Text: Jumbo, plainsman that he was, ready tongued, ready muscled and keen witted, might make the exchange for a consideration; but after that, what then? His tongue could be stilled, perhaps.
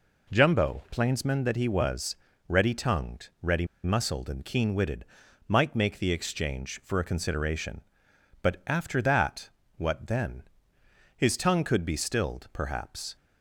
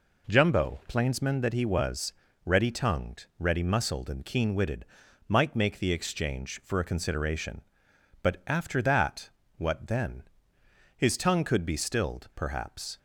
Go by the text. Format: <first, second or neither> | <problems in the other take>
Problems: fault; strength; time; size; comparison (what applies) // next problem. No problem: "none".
second | pauses between "ready" and "muscled"; slight; at 3.6 s; 0.19 s long